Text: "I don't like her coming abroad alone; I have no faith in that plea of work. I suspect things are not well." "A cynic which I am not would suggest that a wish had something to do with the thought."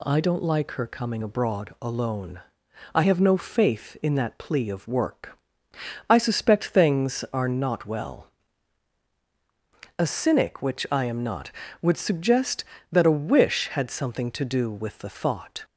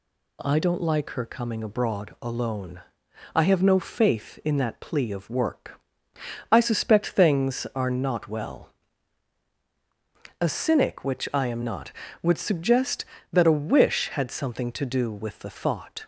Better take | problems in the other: neither | none

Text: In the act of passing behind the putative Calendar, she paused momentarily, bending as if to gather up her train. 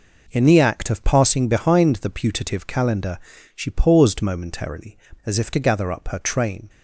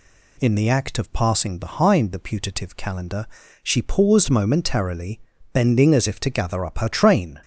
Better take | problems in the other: second | skips "bending"; at 5.1 s

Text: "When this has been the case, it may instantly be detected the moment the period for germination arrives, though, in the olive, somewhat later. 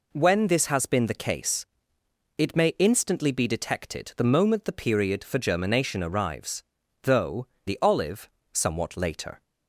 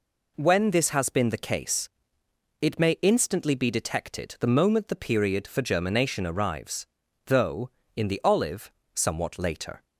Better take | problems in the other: second | skips "in"; at 7.5 s

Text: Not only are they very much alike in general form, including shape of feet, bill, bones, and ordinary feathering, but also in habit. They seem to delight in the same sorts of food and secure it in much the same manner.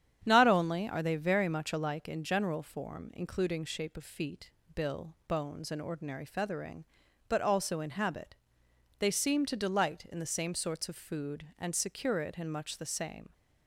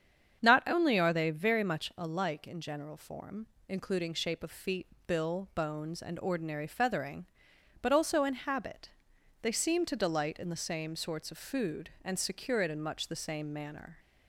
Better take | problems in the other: second | starts louder than the rest; strong; until 1.2 s; 9 dB; strong in the second // stops before "manner"; at 13.3 s

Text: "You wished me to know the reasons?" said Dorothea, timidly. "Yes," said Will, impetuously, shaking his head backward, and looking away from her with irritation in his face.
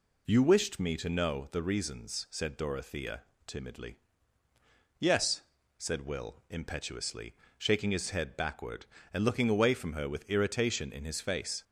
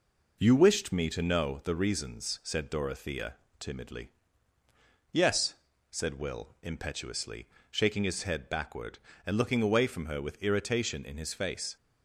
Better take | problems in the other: first | gets quieter; slight; throughout; 2.5 dB

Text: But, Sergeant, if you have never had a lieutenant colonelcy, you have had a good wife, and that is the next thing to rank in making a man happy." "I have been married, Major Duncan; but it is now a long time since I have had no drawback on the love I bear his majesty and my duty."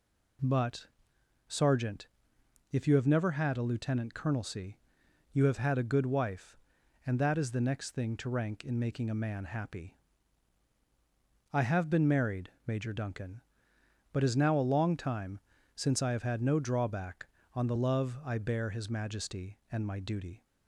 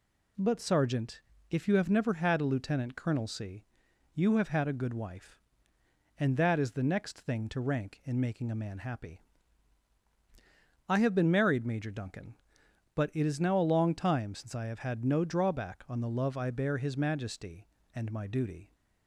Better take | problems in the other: second | skips "it"; at 14.2 s // pauses between "time" and "since"; slight; at 15.3 s; 0.36 s long

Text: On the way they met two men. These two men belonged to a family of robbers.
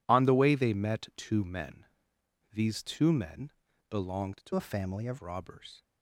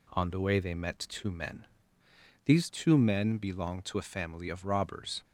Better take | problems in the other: second | pauses between "men" and "belonged"; at 3.5 s; 0.38 s long // changes voice from "a" to "of"; from 4.5 to 5.1 s; 0.6 s long

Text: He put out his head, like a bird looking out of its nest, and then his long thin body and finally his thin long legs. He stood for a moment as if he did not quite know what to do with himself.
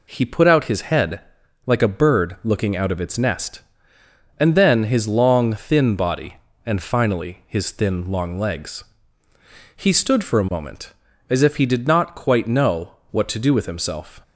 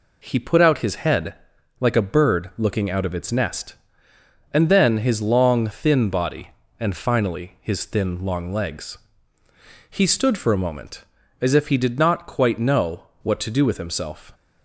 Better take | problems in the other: neither | pauses between "know" and "what"; slight; the same in both

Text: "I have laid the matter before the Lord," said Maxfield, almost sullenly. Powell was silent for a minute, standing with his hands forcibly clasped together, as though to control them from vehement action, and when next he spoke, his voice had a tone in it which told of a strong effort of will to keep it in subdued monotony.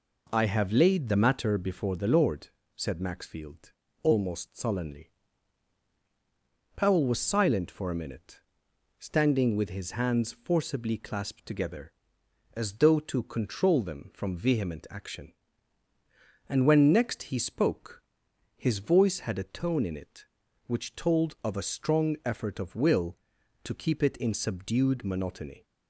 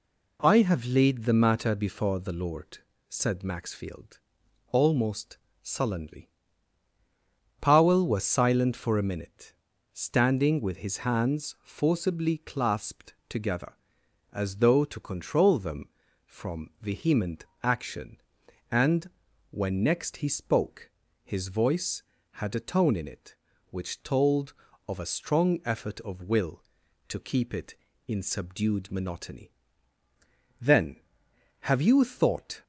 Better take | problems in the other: first | pauses between "almost" and "sullenly"; slight; at 5.3 s; 0.24 s long // pauses between "clasped" and "together"; slight; at 13.1 s; 0.16 s long // pauses between "vehement" and "action"; slight; at 17.4 s; 0.18 s long // pauses between "and" and "when"; at 19.1 s; 0.40 s long // goes on to say "Then have you thought"; strong; from 30.6 s on; 2.0 s long

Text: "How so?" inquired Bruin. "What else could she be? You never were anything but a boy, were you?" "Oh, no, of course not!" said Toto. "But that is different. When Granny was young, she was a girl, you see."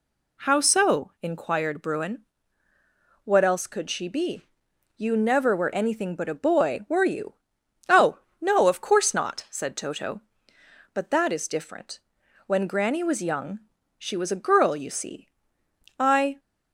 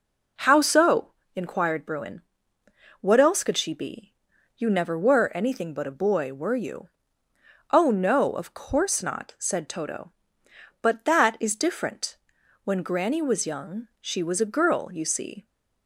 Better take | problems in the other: second | goes on to say "I"; slight; from 15.9 s on; 0.40 s long

